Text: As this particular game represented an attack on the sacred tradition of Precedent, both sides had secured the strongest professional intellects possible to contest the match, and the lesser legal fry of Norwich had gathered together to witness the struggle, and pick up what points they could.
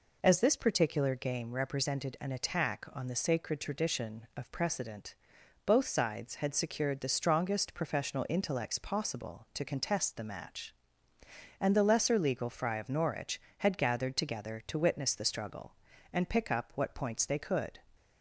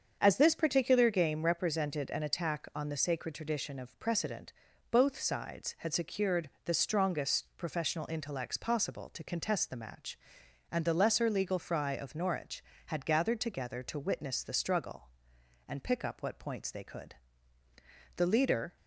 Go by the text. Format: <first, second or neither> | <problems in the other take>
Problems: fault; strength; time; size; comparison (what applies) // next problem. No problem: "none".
first | starts louder than the rest; until 1.2 s; 7 dB // pauses between "secured" and "the"; slight; at 6.4 s; 0.16 s long // goes on to say "The leader"; from 18.1 s on; 0.60 s long